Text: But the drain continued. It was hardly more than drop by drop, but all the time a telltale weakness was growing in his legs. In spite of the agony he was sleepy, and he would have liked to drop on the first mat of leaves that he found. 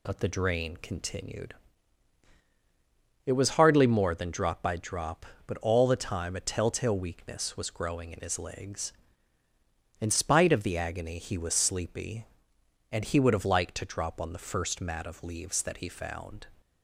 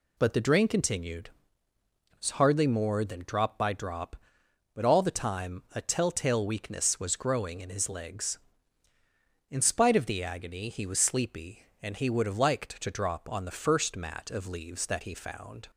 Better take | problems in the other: neither | none

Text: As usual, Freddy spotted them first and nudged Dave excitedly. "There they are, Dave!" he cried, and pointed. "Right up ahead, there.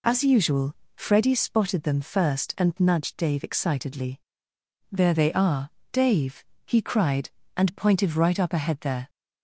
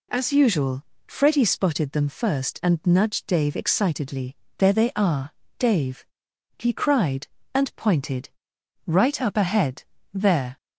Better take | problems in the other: neither | none

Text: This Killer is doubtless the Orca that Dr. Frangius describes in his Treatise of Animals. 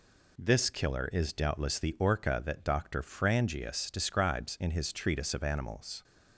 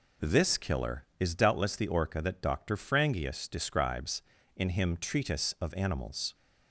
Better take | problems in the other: first | says "him" for "his"; at 4.7 s

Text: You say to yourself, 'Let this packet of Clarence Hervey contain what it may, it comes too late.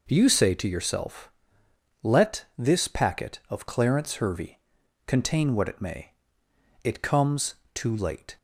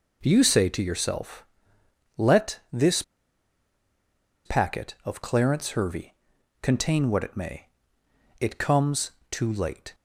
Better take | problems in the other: first | pauses between "this" and "packet"; strong; at 3.0 s; 1.4 s long // pauses between "Hervey" and "contain"; noticeable; at 6.1 s; 0.46 s long; noticeable in the first // pauses between "comes" and "too"; slight; at 9.1 s; 0.18 s long; slight in the first

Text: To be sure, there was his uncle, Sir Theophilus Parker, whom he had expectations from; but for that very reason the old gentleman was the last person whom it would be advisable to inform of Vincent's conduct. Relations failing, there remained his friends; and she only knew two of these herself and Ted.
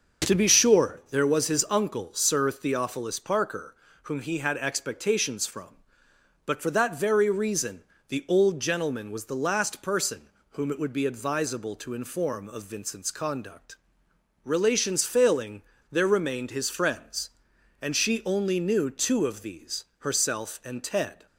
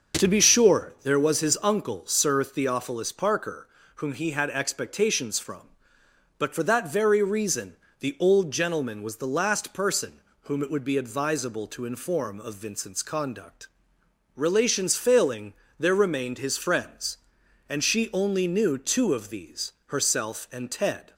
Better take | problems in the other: neither | starts louder than the rest; the same in both // pauses between "reason" and "the"; slight; the same in both // pauses between "person" and "whom"; slight; the same in both

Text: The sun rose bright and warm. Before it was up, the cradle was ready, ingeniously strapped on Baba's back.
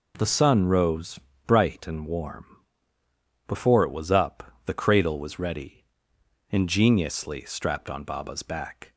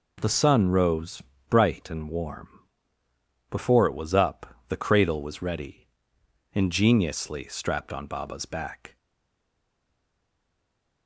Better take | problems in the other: first | pauses between "rose" and "bright"; slight; at 1.2 s; 0.26 s long; slight in the first // stays silent after the last word; from 8.9 s on; 2.1 s long

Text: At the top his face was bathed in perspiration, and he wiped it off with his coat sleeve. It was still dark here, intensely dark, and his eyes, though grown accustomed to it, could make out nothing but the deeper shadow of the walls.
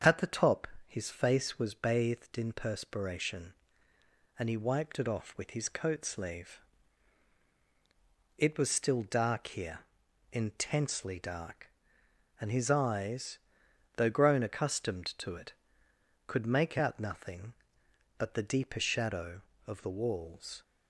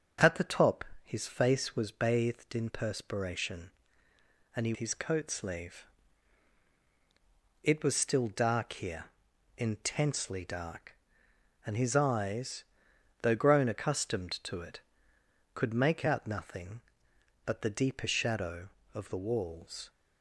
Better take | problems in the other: first | starts louder than the rest; until 1.4 s; 7 dB; strong in the first // pauses between "top" and "his"; slight; at 0.8 s; 0.22 s long; slight in the first // skips "wiped it off with"; at 4.7 s

